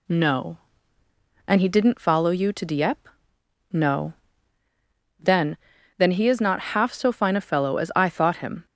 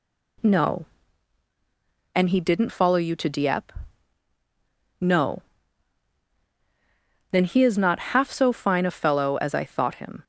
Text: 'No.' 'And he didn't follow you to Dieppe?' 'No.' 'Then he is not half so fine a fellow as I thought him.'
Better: second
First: says "Then" twice; at 5.9 s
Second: none

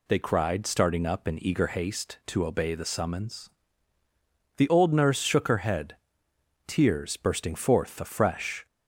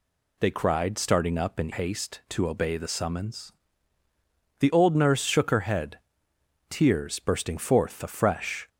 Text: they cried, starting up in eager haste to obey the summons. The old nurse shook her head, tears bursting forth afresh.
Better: first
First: none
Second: skips "eager"; at 1.7 s

